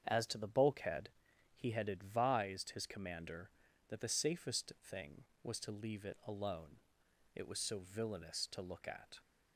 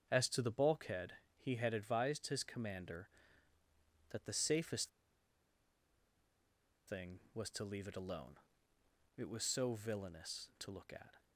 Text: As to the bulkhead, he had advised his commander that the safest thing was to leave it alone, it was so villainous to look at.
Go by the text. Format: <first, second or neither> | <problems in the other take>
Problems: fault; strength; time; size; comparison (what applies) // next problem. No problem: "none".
first | starts louder than the rest; until 1.1 s; 7 dB; strong in the first // pauses between "safest" and "thing"; strong; at 4.8 s; 1.9 s long